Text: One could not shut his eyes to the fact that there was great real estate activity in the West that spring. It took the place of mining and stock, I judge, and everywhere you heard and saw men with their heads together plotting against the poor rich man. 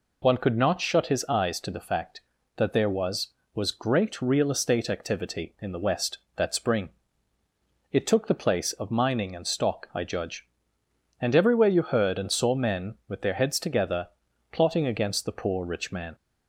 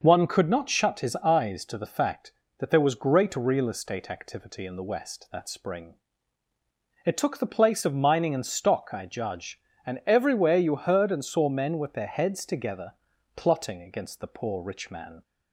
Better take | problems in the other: second | says "was" twice; at 3.5 s // pauses between "together" and "plotting"; noticeable; at 14.0 s; 0.46 s long; also in the second

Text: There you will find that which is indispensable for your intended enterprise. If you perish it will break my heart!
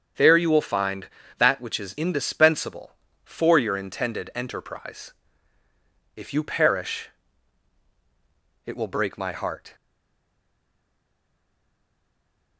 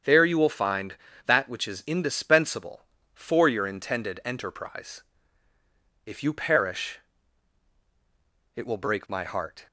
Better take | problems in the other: second | starts louder than the rest; strong; until 1.4 s; 8 dB; strong in the second // pauses between "perish" and "it"; strong; at 7.0 s; 1.5 s long; strong in the second // stays silent after the last word; strong; from 9.7 s on; 2.8 s long

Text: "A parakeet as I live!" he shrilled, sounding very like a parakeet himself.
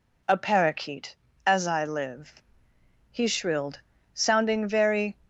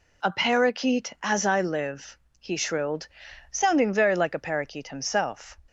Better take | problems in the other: second | stops before "like a parakeet himself"; at 5.2 s

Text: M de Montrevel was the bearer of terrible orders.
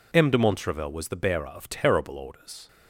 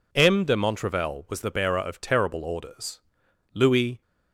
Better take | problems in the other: first | goes on to say "Louis"; slight; from 3.5 s on; 0.48 s long

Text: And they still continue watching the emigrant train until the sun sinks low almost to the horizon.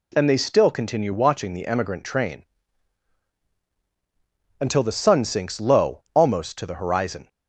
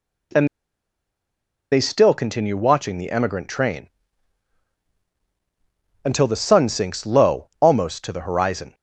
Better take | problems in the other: first | pauses between "And" and "they"; at 0.4 s; 1.2 s long // pauses between "train" and "until"; strong; at 3.8 s; 2.1 s long; strong in the first

